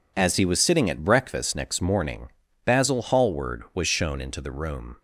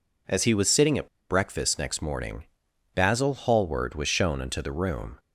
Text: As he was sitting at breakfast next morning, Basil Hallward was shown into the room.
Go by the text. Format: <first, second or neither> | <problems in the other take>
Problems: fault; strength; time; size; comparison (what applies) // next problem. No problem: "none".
first | pauses between "at" and "breakfast"; slight; at 1.0 s; 0.21 s long